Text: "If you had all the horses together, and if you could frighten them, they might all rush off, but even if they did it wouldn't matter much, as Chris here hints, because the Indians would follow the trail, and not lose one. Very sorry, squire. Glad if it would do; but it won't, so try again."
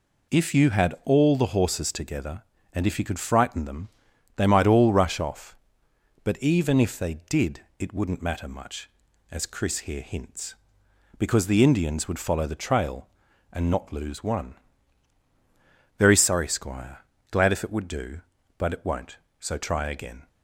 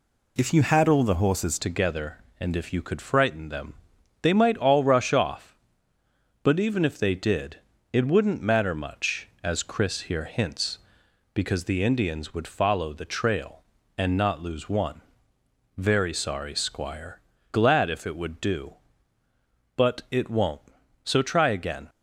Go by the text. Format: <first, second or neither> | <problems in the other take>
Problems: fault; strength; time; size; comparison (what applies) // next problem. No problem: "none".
first | changes voice at "together"; from 1.5 s on; 20.3 s long // pauses between "did" and "it"; slight; at 7.5 s; 0.36 s long; slight in the first